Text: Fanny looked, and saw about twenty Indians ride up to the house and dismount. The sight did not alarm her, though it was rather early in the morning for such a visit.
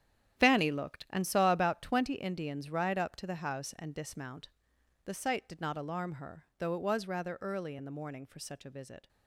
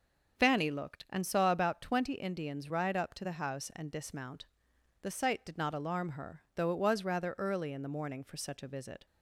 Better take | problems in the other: second | gets quieter; strong; throughout; 12 dB // starts louder than the rest; strong; until 1.4 s; 10.5 dB; also in the second

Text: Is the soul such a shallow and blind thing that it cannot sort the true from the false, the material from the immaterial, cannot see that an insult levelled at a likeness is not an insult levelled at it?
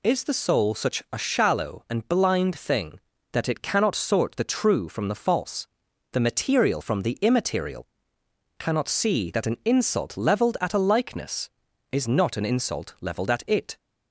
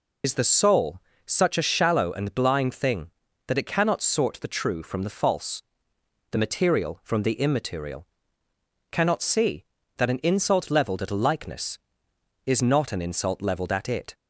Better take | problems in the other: first | loses the start of "Is"; at 0.2 s; 75 ms // pauses between "soul" and "such"; slight; at 1.0 s; 0.24 s long

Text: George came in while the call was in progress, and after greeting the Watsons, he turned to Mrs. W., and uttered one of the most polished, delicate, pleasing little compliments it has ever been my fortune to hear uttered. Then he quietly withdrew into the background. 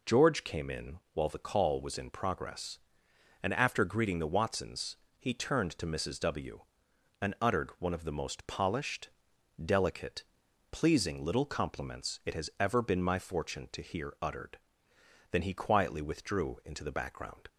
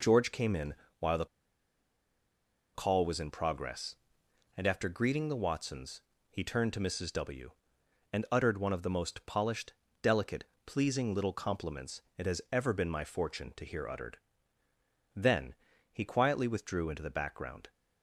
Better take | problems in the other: first | pauses between "in" and "while"; slight; at 0.7 s; 0.24 s long // pauses between "the" and "call"; strong; at 1.2 s; 1.4 s long // pauses between "compliments" and "it"; slight; at 12.0 s; 0.16 s long // pauses between "Then" and "he"; slight; at 15.5 s; 0.36 s long

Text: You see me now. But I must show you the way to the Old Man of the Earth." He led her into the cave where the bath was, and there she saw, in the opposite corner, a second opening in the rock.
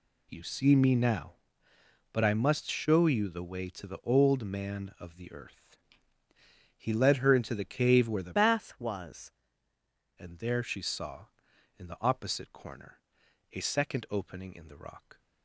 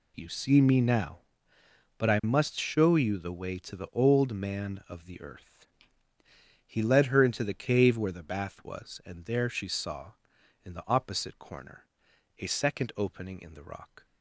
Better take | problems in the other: second | changes voice from "bath" to "was"; from 8.3 to 9.2 s; 0.9 s long

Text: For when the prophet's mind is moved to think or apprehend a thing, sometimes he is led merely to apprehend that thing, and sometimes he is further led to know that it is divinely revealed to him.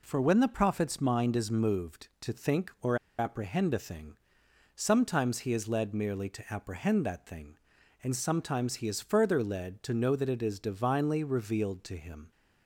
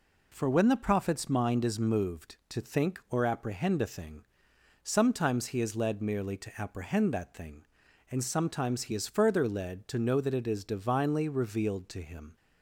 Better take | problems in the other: second | pauses between "or" and "apprehend"; slight; at 2.9 s; 0.20 s long

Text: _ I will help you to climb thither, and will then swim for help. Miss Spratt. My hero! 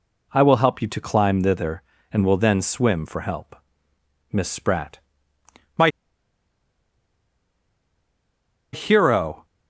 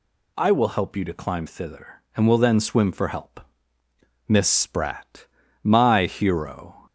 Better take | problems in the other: second | pauses between "My" and "hero"; strong; at 5.8 s; 2.8 s long

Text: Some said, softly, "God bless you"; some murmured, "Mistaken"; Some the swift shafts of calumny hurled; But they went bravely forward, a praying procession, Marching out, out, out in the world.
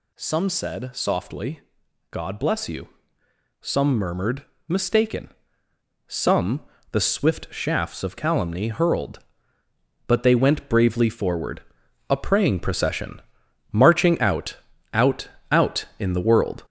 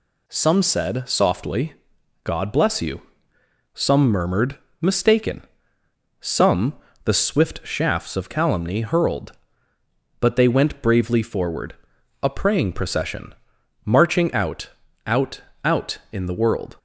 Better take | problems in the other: second | gets louder; noticeable; throughout; 5 dB // pauses between "Some" and "the"; slight; at 6.6 s; 0.30 s long; slight in the second

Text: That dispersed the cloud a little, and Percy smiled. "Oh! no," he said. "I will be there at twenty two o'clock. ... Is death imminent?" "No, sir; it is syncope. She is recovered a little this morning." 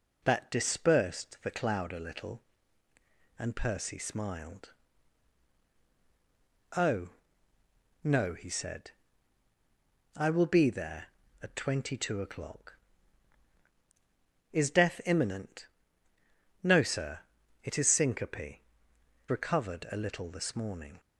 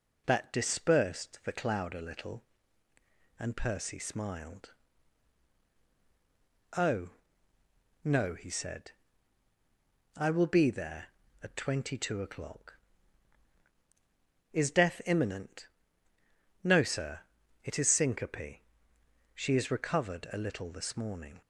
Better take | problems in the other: second | skips "She is"; at 18.9 s

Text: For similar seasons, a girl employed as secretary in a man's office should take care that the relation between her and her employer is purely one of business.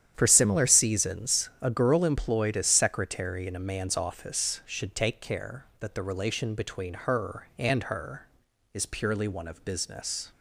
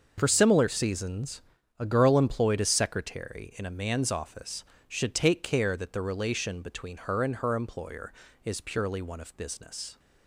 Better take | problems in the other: second | starts louder than the rest; strong; until 1.1 s; 10 dB; also in the second // skips "employer"; at 8.4 s

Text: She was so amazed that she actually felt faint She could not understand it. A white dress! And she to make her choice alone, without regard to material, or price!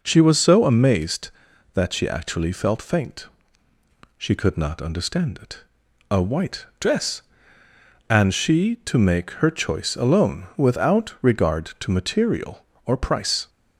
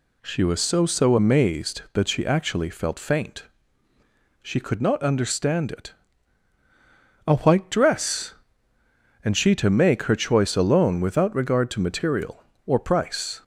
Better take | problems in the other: first | says "so" twice; at 0.8 s // pauses between "faint" and "She"; noticeable; at 3.4 s; 0.96 s long; noticeable in the first

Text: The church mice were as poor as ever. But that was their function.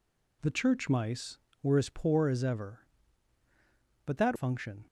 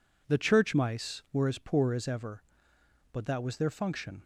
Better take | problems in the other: second | skips "was their"; at 4.3 s

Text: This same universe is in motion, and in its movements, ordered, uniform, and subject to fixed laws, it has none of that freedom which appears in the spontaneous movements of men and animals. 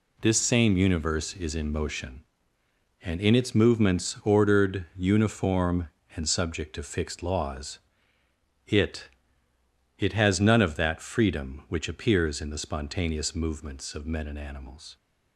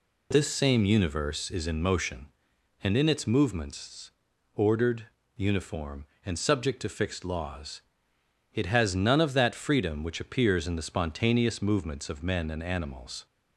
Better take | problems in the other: second | says "it" twice; at 9.9 s

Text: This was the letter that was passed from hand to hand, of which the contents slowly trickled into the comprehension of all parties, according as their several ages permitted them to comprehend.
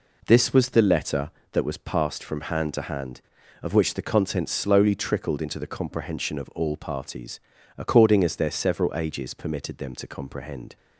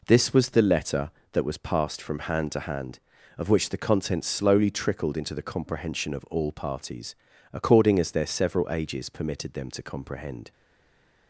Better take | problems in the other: first | stays silent after the last word; slight; from 10.5 s on; 0.7 s long

